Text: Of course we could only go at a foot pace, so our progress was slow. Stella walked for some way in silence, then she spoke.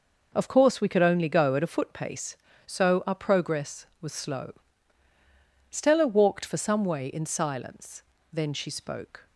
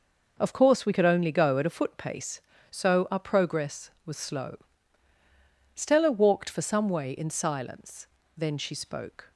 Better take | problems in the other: neither | none

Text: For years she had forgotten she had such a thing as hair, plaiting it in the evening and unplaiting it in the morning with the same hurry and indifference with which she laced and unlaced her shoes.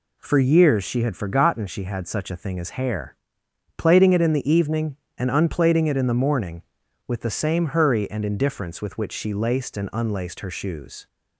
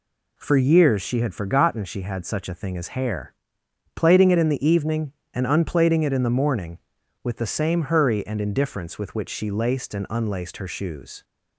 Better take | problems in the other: neither | none

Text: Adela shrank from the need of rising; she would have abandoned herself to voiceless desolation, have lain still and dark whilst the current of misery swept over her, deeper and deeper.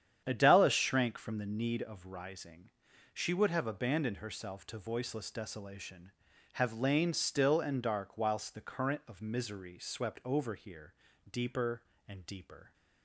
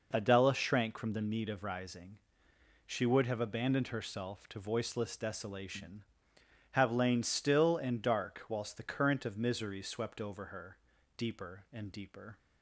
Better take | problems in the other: second | starts louder than the rest; strong; until 1.2 s; 9 dB // says "here" for "her"; at 10.5 s

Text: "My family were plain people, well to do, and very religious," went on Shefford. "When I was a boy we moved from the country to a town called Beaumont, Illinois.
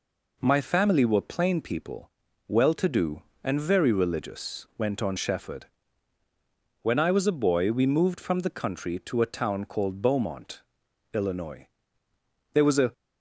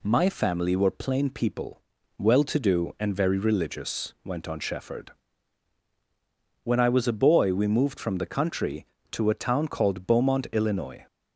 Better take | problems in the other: second | goes on to say "There was a"; slight; from 12.5 s on; 0.40 s long

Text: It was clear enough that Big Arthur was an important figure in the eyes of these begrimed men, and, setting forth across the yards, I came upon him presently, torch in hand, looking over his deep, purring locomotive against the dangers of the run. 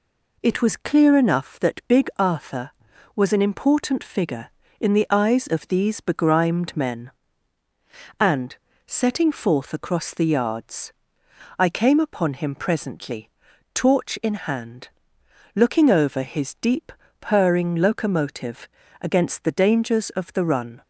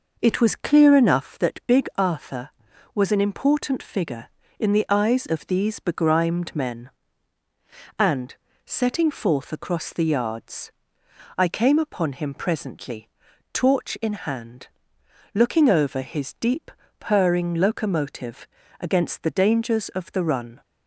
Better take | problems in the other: first | starts louder than the rest; noticeable; until 1.5 s; 5.5 dB // pauses between "locomotive" and "against"; slight; at 18.4 s; 0.34 s long; slight in the first

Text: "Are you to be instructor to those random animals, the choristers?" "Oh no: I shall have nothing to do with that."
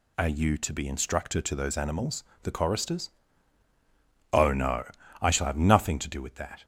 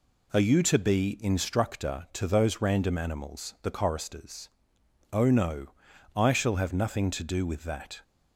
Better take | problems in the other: second | skips "random"; at 1.7 s

